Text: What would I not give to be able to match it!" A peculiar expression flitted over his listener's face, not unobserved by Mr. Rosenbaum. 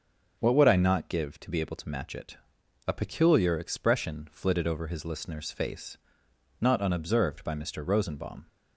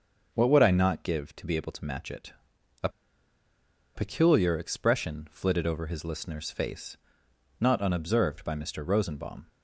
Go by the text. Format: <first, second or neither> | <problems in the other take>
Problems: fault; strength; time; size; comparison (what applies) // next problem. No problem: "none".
first | starts louder than the rest; until 1.3 s; 6.5 dB; also in the first // pauses between "A" and "peculiar"; at 2.8 s; 1.0 s long